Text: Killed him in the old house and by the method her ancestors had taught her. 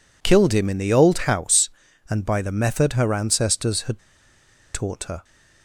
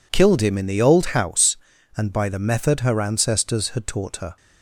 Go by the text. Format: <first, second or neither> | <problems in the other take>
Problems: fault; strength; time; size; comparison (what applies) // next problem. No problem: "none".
second | pauses between "had" and "taught"; noticeable; at 4.0 s; 0.73 s long